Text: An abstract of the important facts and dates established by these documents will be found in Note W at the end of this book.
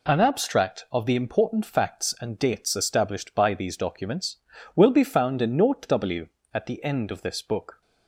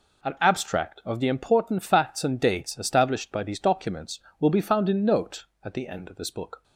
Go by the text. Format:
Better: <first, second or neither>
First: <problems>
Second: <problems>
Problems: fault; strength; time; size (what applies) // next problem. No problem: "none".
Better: first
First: none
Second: skips "W"; at 5.5 s